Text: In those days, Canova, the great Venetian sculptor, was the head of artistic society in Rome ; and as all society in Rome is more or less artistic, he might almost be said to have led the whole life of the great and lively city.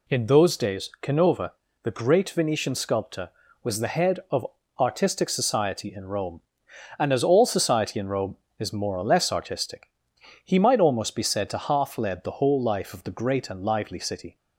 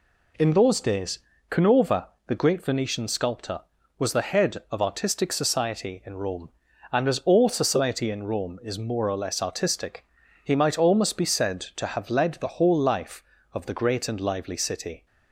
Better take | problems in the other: second | pauses between "of" and "artistic"; slight; at 4.4 s; 0.32 s long // says "half" for "have"; at 11.5 s

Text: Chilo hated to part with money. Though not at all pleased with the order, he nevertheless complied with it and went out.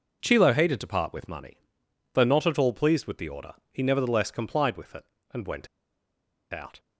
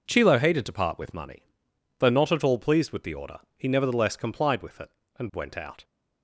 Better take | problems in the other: second | pauses between "went" and "out"; noticeable; at 5.6 s; 0.84 s long

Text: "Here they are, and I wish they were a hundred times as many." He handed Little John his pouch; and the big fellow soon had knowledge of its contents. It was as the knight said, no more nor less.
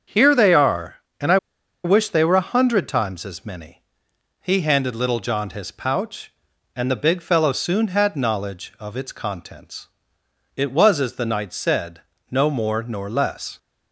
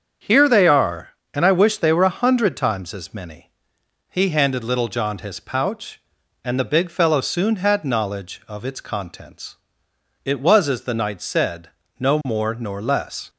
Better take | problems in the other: second | starts louder than the rest; strong; until 1.3 s; 7.5 dB; strong in the second // pauses between "I" and "wish"; noticeable; at 1.3 s; 0.47 s long

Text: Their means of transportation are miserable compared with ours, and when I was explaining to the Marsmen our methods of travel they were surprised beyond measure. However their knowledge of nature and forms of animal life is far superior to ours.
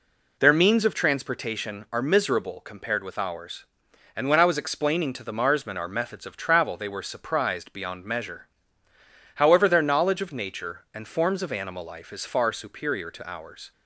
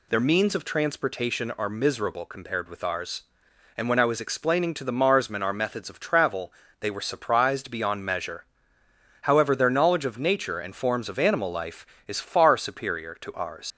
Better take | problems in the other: first | pauses between "travel" and "they"; slight; at 6.5 s; 0.28 s long // leaves "ours" unfinished; at 13.7 s; 90 ms

